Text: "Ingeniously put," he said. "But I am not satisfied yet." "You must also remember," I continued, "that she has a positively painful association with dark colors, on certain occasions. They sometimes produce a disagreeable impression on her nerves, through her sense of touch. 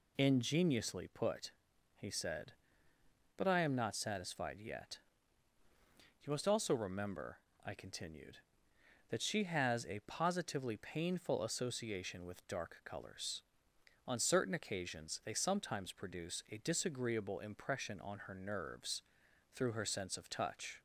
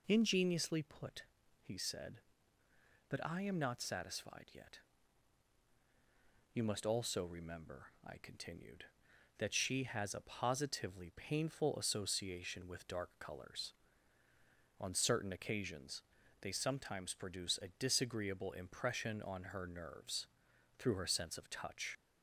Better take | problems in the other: first | leaves "touch" unfinished; at 21.9 s; 40 ms

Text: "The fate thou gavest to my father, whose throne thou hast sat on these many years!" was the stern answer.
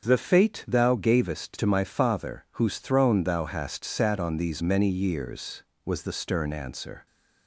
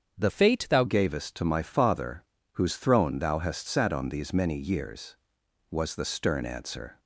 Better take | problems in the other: first | starts louder than the rest; strong; until 1.2 s; 7.5 dB; also in the first // changes voice from "fate" to "thou"; from 0.2 to 0.8 s; 0.6 s long

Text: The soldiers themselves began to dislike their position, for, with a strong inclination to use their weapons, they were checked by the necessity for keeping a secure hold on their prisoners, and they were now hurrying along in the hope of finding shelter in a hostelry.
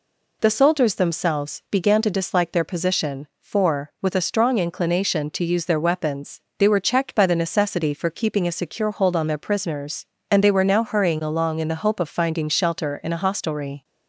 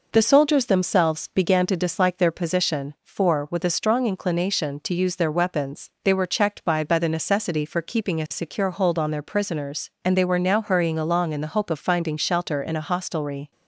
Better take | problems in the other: first | says "by" twice; at 6.8 s

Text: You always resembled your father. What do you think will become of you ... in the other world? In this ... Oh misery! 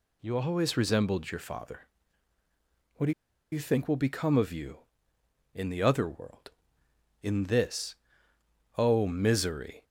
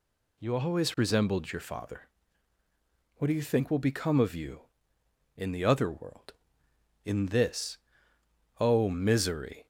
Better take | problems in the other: second | pauses between "do" and "you"; at 3.1 s; 0.38 s long

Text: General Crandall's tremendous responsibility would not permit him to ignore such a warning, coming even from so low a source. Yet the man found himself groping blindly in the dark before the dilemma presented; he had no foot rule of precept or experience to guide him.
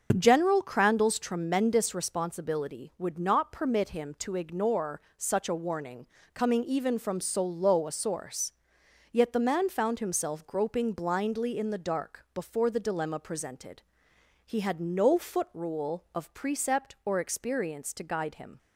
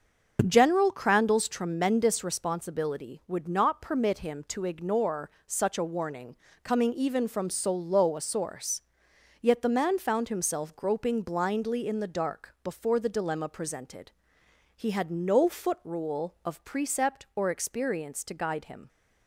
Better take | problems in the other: neither | starts louder than the rest; the same in both // pauses between "ignore" and "such"; slight; the same in both

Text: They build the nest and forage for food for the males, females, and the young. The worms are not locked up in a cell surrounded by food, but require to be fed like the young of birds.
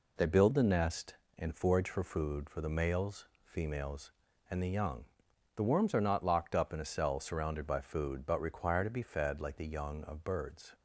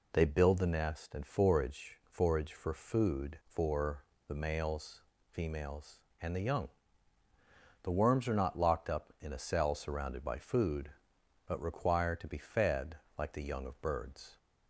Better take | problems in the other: first | says "forage" twice; at 2.0 s // pauses between "for" and "the"; slight; at 4.0 s; 0.24 s long // pauses between "fed" and "like"; slight; at 12.9 s; 0.24 s long

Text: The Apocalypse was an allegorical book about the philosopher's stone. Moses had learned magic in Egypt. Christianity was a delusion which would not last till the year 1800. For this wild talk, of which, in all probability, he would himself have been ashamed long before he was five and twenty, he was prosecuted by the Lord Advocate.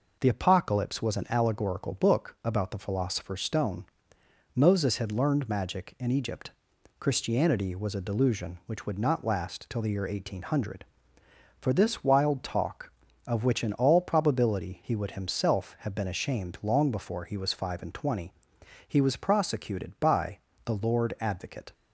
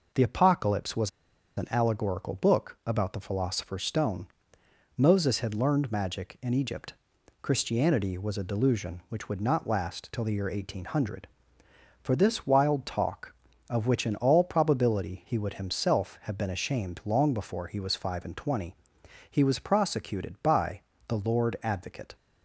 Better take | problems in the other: first | pauses between "was" and "an"; noticeable; at 1.0 s; 0.47 s long // pauses between "by" and "the"; slight; at 20.8 s; 0.26 s long; slight in the first

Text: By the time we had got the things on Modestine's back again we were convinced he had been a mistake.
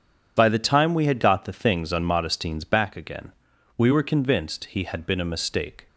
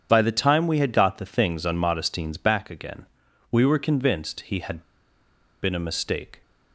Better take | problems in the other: first | starts louder than the rest; strong; until 1.1 s; 8 dB // pauses between "again" and "we"; noticeable; at 3.0 s; 0.48 s long; noticeable in the first // pauses between "had" and "been"; noticeable; at 4.8 s; 0.79 s long

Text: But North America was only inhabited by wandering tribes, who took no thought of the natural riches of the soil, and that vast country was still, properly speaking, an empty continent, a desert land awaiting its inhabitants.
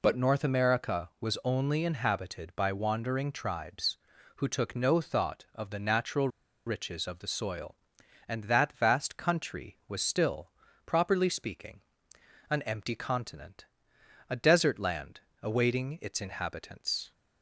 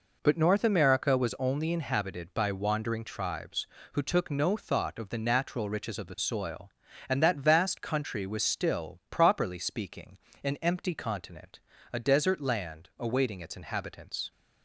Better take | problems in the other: second | pauses between "natural" and "riches"; at 6.2 s; 0.38 s long // pauses between "land" and "awaiting"; slight; at 15.2 s; 0.22 s long

